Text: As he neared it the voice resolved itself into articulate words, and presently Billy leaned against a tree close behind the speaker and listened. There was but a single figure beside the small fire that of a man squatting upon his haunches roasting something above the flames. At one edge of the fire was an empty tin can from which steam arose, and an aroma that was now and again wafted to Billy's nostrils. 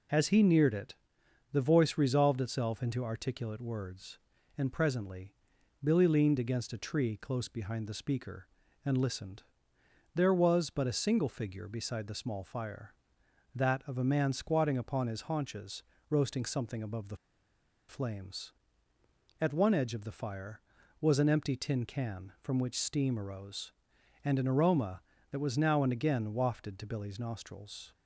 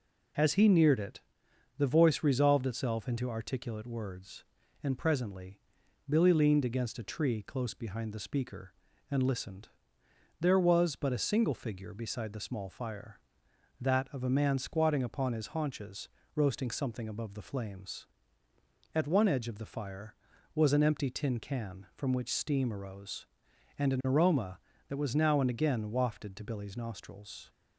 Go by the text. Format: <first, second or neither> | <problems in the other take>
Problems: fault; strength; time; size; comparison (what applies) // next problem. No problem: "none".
second | pauses between "it" and "the"; noticeable; at 0.9 s; 0.58 s long; noticeable in the second // pauses between "presently" and "Billy"; noticeable; at 5.3 s; 0.50 s long; noticeable in the second // pauses between "haunches" and "roasting"; slight; at 15.8 s; 0.24 s long; slight in the second // pauses between "the" and "flames"; noticeable; at 17.1 s; 0.72 s long